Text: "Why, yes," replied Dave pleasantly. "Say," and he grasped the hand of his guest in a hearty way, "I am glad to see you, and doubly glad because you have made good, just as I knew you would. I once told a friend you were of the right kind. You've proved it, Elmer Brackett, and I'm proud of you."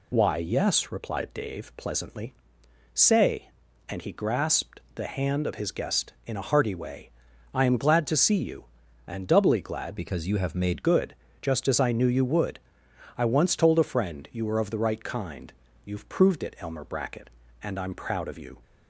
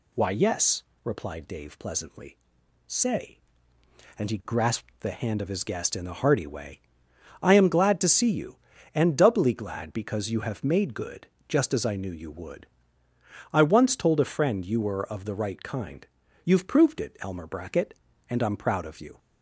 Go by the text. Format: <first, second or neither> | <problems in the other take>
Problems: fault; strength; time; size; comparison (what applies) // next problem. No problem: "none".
second | changes voice from "because" to "made"; from 9.9 to 10.8 s; 0.9 s long